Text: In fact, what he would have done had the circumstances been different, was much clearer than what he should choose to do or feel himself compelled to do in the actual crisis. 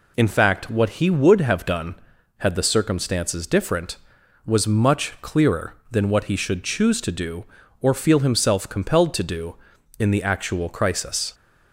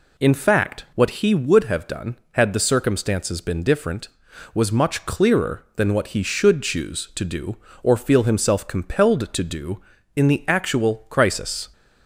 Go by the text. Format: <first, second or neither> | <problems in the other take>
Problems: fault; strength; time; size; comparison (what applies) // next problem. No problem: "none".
second | skips "been"; at 3.4 s